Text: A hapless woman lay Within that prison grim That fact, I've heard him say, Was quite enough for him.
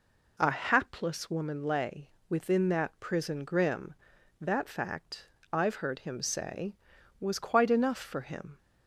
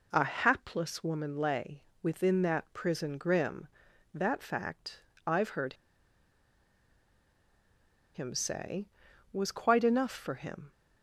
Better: first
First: pauses between "lay" and "Within"; slight; at 2.1 s; 0.18 s long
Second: pauses between "lay" and "Within"; slight; at 1.8 s; 0.18 s long // pauses between "heard" and "him"; strong; at 5.7 s; 2.3 s long

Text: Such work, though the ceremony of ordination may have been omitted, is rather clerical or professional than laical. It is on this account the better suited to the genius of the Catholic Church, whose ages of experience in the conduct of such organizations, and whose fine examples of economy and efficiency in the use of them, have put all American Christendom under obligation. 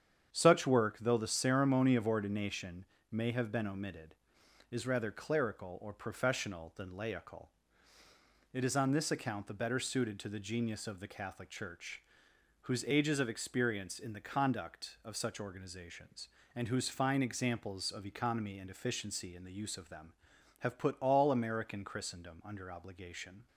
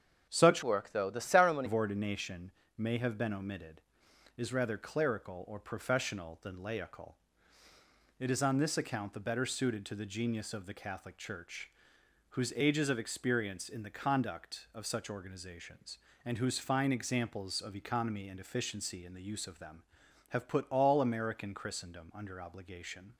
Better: first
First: starts louder than the rest; strong; until 1.3 s; 8 dB // pauses between "ordination" and "may"; slight; at 2.8 s; 0.26 s long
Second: starts louder than the rest; strong; until 1.3 s; 7.5 dB // changes voice from "work" to "ceremony"; from 0.6 to 1.6 s; 1.0 s long // pauses between "ordination" and "may"; slight; at 2.5 s; 0.26 s long

